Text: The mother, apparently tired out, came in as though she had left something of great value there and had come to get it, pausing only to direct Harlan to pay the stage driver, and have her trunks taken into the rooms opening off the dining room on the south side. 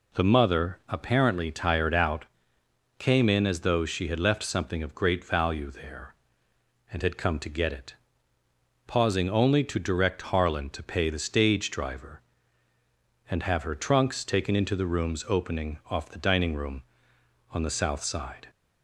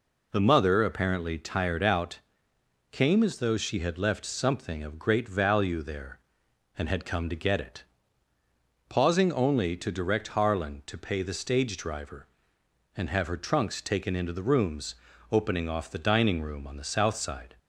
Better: first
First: none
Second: skips "in"; at 3.2 s // pauses between "rooms" and "opening"; at 14.9 s; 0.38 s long

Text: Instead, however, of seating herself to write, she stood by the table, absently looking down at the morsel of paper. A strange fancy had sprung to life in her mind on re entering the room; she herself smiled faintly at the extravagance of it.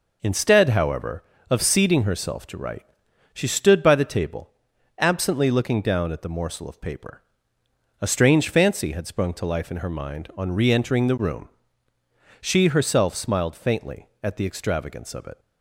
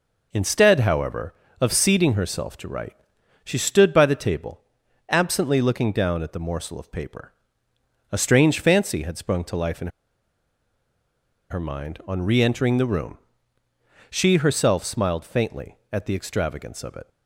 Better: first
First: none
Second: pauses between "in" and "her"; strong; at 9.8 s; 1.6 s long

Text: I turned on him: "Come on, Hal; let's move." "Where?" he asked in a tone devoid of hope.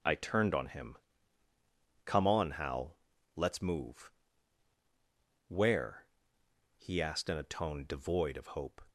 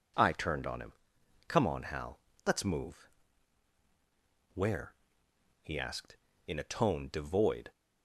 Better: first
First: none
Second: stops before "of hope"; at 7.7 s

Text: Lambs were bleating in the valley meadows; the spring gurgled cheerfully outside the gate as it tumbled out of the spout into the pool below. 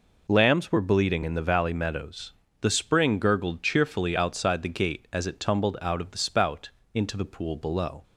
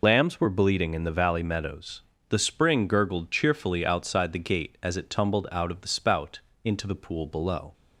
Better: first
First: pauses between "spout" and "into"; slight; at 6.6 s; 0.24 s long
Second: loses the start of "Lambs"; at 0.0 s; 55 ms // pauses between "spout" and "into"; slight; at 6.3 s; 0.24 s long

